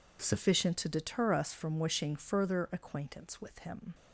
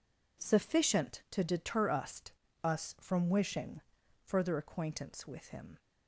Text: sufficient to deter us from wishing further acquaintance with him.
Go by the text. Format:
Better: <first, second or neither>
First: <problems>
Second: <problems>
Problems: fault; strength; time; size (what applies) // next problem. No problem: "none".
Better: first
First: none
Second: says "us" twice; at 2.6 s // pauses between "wishing" and "further"; at 3.8 s; 0.42 s long